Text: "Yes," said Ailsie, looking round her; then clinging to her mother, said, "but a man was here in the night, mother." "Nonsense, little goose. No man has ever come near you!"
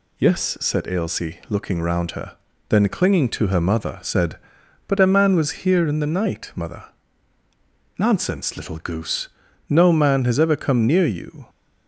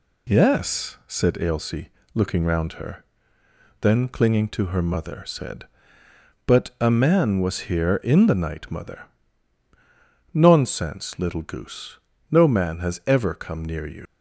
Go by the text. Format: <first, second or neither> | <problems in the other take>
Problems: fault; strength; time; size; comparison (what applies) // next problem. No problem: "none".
first | leaves "you" unfinished; at 14.0 s; 105 ms